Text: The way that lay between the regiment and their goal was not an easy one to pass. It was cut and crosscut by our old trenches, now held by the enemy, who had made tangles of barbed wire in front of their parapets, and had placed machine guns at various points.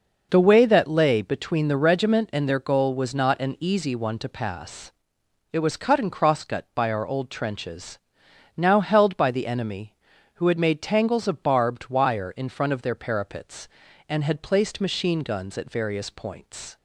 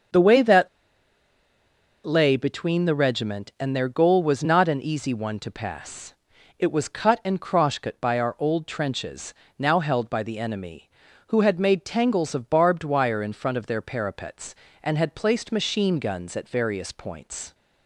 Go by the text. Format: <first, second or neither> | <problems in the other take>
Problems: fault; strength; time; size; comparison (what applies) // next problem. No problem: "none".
first | starts louder than the rest; until 2.5 s; 7 dB // pauses between "that" and "lay"; strong; at 0.6 s; 1.3 s long